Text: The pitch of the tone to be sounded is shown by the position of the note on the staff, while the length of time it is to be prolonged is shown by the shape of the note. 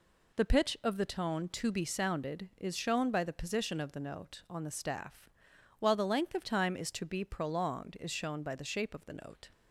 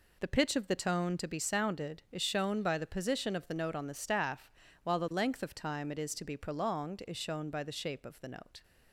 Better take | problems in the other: second | skips "it"; at 6.7 s

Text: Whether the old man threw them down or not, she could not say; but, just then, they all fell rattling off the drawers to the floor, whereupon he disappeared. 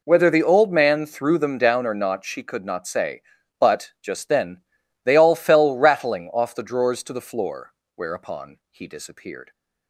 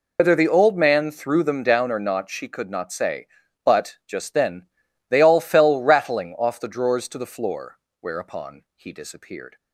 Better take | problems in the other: first | loses the start of "Whether"; at 0.1 s; 100 ms

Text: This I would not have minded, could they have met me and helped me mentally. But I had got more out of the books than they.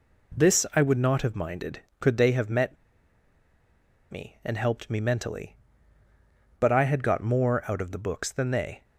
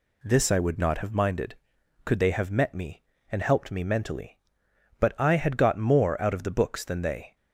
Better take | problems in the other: second | pauses between "met" and "me"; strong; at 2.7 s; 1.3 s long

